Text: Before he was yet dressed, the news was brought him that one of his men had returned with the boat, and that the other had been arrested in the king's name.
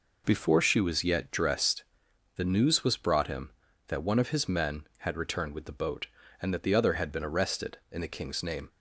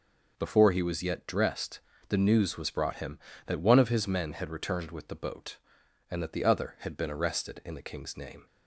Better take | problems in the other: second | says "she" for "he"; at 0.5 s

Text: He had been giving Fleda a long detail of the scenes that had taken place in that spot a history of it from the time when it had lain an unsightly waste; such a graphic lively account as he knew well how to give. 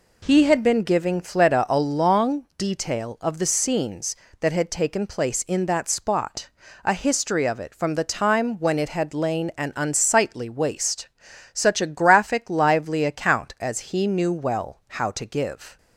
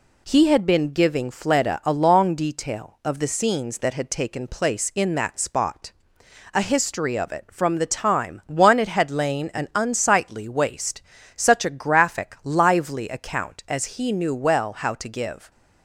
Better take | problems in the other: first | pauses between "spot" and "a"; noticeable; at 5.9 s; 0.64 s long; slight in the first // says "one" for "when"; at 8.4 s

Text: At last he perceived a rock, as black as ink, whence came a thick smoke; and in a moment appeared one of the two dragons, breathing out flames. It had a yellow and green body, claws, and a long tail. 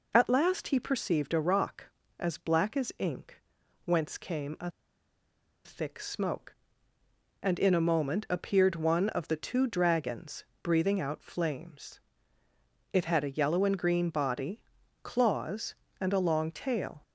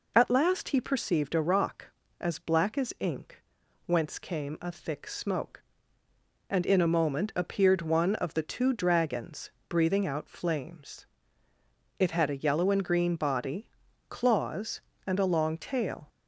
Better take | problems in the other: second | pauses between "a" and "thick"; noticeable; at 4.7 s; 0.94 s long

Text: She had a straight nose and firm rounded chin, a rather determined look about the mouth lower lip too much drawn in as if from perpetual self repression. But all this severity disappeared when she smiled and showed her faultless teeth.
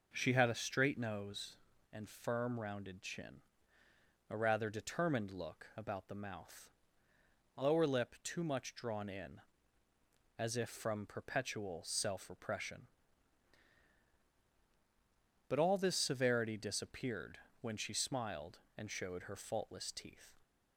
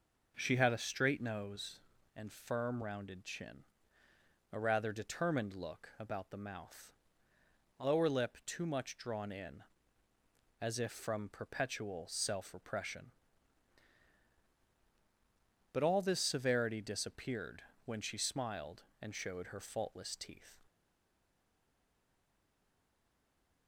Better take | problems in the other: first | pauses between "mouth" and "lower"; noticeable; at 6.9 s; 0.86 s long; noticeable in the first // pauses between "disappeared" and "when"; slight; at 17.6 s; 0.22 s long; slight in the first // stays silent after the last word; strong; from 20.6 s on; 3.0 s long

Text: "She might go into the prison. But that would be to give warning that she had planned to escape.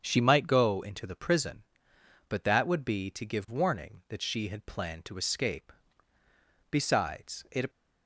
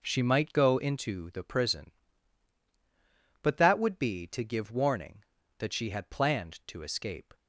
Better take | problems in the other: second | starts louder than the rest; strong; until 1.0 s; 7.5 dB // goes on to say "Besides it"; noticeable; from 6.7 s on; 0.98 s long

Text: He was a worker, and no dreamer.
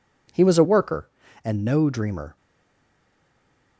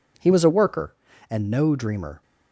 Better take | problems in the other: second | stays silent after the last word; noticeable; from 2.3 s on; 1.4 s long

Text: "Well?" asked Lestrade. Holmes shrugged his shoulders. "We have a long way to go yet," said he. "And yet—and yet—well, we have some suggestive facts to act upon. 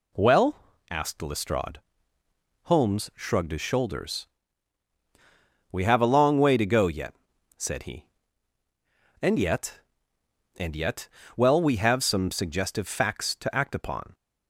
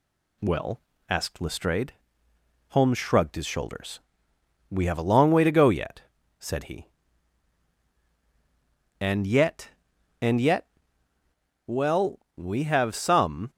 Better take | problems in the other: first | stops before "suggestive facts to act upon"; at 13.5 s

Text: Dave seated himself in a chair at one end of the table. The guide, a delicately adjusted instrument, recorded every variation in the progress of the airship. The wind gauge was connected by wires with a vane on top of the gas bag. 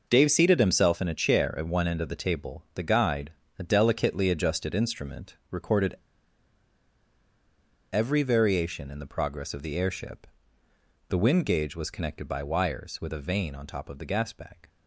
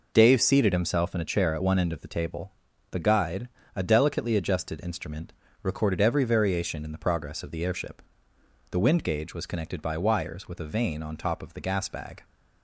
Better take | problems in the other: second | pauses between "recorded" and "every"; strong; at 5.9 s; 1.9 s long

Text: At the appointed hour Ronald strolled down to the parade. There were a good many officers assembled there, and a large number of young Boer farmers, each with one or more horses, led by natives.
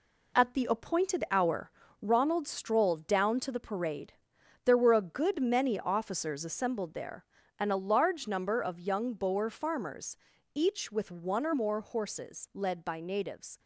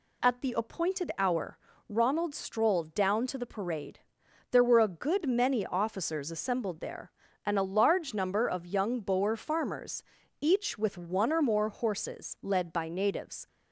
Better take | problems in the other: second | gets quieter; strong; throughout; 7.5 dB // pauses between "hour" and "Ronald"; slight; at 1.6 s; 0.32 s long; slight in the second

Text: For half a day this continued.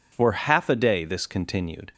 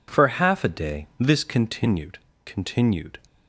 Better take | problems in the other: first | says "continued" twice; at 2.4 s

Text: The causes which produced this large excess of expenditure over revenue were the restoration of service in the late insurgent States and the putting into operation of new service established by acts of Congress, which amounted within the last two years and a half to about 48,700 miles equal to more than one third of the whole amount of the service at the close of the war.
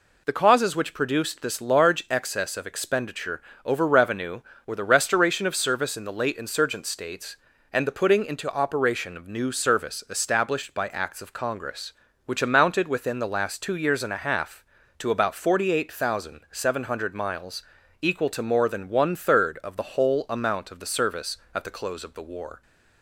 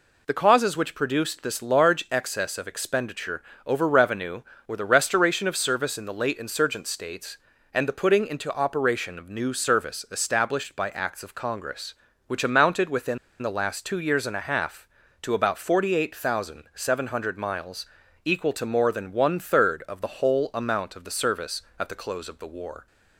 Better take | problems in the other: first | pauses between "expenditure" and "over"; slight; at 3.4 s; 0.24 s long; slight in the first // pauses between "within" and "the"; slight; at 13.1 s; 0.24 s long // pauses between "miles" and "equal"; at 17.8 s; 0.38 s long; also in the first

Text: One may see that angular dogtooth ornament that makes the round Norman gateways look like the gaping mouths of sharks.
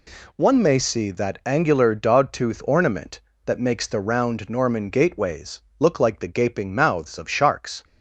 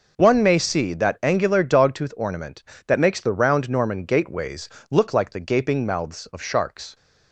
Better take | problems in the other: neither | pauses between "gateways" and "look"; slight; the same in both

